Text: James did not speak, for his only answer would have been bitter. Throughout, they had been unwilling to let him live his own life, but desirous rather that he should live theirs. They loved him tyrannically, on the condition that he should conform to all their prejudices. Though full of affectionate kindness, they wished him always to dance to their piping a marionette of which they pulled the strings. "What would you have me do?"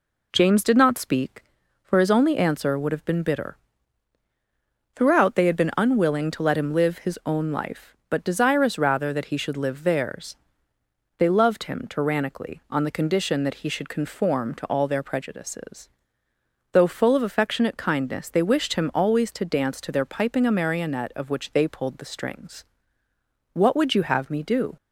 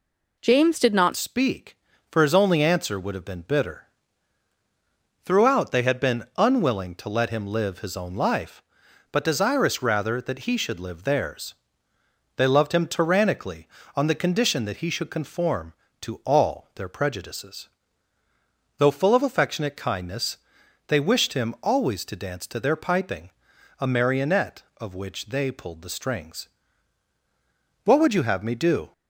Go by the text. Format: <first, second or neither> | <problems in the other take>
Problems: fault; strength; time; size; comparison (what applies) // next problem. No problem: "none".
first | changes voice at "speak"; from 1.1 s on; 27.8 s long // pauses between "piping" and "a"; noticeable; at 23.3 s; 0.48 s long